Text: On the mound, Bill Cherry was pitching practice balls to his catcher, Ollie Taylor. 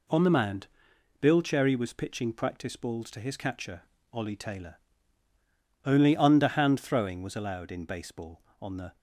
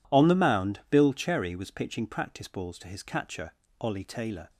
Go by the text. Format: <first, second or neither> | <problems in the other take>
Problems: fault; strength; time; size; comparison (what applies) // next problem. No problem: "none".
second | goes on to say "Only underhand throwing was allowed in baseball on the"; strong; from 5.8 s on; 3.1 s long